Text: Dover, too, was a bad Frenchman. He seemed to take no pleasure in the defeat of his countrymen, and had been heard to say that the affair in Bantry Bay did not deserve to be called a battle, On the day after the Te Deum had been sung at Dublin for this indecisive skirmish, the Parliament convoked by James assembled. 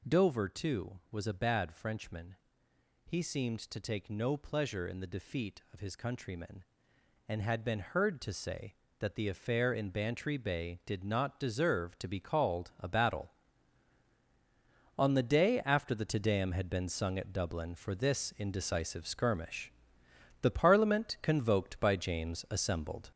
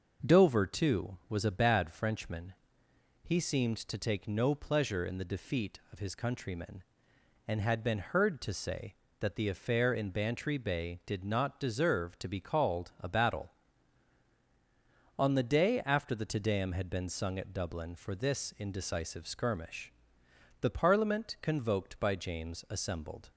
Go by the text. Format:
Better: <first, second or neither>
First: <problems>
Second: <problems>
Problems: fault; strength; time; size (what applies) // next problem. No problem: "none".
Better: second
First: gets louder; noticeable; throughout; 6 dB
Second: none